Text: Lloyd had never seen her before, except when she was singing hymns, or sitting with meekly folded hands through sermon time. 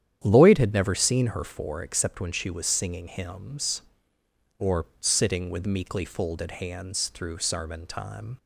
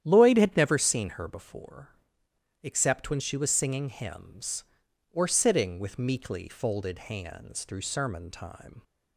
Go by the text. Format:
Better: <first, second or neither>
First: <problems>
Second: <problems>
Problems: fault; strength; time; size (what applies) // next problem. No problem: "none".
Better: second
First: starts louder than the rest; strong; until 1.2 s; 10 dB // says "for" for "before"; at 1.4 s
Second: starts louder than the rest; strong; until 1.0 s; 10.5 dB